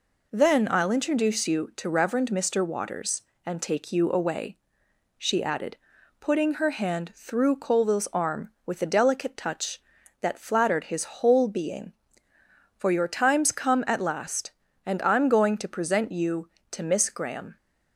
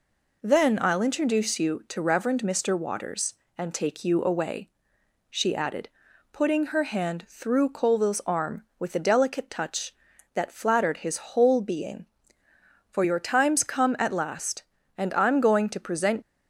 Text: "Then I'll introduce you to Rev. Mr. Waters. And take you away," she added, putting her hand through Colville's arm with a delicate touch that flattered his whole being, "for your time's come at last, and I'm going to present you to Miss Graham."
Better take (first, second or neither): first